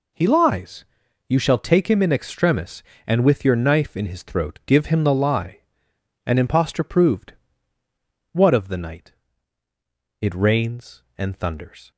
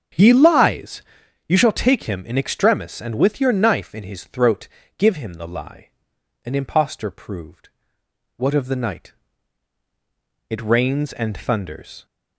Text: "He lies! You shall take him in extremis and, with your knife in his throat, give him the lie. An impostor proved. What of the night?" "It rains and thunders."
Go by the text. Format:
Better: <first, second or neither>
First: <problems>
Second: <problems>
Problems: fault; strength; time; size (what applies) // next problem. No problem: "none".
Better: first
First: none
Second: starts louder than the rest; strong; until 1.4 s; 7 dB